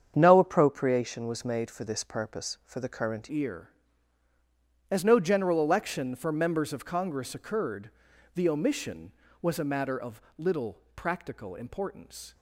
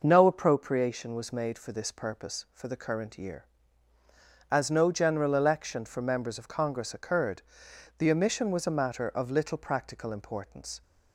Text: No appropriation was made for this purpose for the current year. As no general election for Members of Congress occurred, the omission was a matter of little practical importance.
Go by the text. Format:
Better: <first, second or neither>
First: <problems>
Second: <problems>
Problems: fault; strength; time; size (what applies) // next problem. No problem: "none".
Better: second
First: starts louder than the rest; strong; until 1.1 s; 8 dB // changes voice at "year"; from 3.3 s on; 9.0 s long // pauses between "of" and "little"; slight; at 10.1 s; 0.16 s long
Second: none